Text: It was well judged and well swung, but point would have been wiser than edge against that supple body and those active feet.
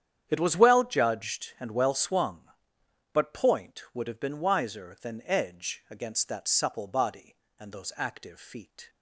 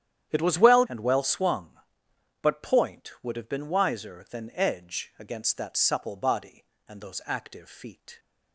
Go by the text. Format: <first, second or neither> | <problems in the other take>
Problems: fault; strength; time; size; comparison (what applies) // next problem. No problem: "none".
first | starts louder than the rest; strong; until 1.3 s; 10 dB; strong in the first // skips "judged"; at 0.8 s